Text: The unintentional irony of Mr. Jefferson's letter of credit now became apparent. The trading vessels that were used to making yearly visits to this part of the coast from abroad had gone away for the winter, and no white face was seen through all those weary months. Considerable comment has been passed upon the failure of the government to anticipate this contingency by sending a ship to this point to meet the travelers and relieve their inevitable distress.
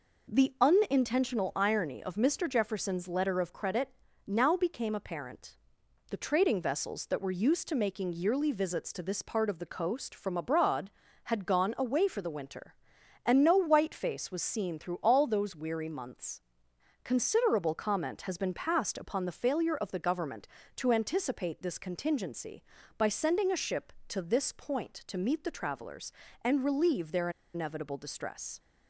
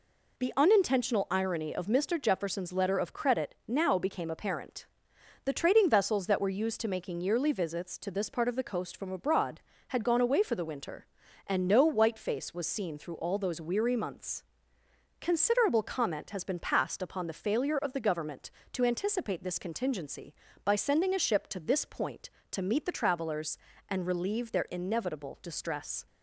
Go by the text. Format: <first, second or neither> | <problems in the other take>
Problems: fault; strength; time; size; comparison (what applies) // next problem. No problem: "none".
second | pauses between "credit" and "now"; at 3.8 s; 0.38 s long // pauses between "their" and "inevitable"; slight; at 27.3 s; 0.23 s long